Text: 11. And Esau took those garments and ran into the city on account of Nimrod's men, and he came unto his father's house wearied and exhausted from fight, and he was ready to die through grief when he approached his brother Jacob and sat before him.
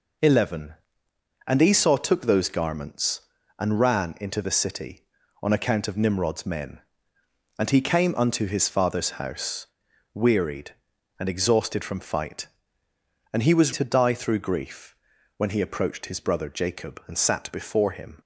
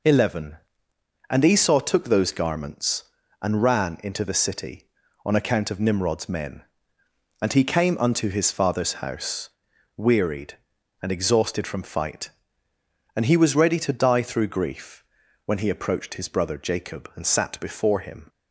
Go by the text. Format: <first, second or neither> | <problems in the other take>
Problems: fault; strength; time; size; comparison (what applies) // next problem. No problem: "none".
second | pauses between "house" and "wearied"; noticeable; at 9.6 s; 0.48 s long; noticeable in the second // skips "ready"; at 13.7 s // pauses between "grief" and "when"; at 14.9 s; 0.44 s long; also in the second